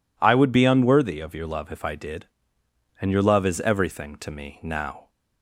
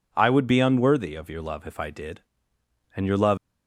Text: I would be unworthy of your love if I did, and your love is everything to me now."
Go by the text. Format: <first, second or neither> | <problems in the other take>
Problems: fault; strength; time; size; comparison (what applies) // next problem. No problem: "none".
first | stops before "is everything to me now"; at 3.3 s